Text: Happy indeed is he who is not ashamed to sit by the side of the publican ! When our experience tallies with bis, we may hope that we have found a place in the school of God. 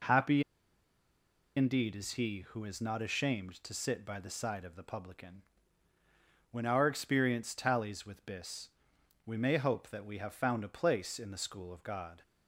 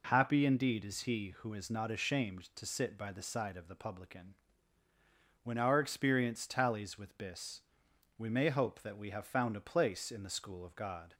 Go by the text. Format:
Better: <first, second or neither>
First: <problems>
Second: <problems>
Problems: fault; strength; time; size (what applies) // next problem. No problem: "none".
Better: second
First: pauses between "Happy" and "indeed"; at 0.4 s; 1.1 s long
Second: none